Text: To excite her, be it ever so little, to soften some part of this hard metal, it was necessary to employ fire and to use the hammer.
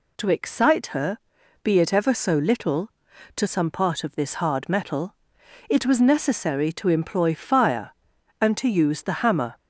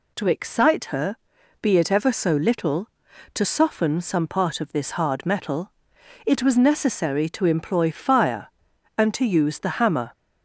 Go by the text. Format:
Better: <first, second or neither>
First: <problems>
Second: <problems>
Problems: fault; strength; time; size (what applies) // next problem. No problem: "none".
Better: second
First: skips "soften"; at 3.4 s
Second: none